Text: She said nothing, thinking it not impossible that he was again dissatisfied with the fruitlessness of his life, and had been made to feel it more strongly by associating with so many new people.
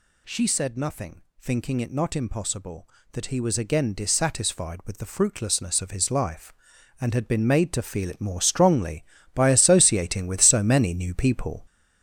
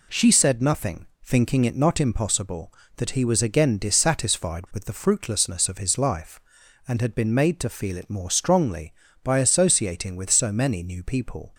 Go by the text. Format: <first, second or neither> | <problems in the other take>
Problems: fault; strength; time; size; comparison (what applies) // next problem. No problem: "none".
second | gets louder; throughout; 6.5 dB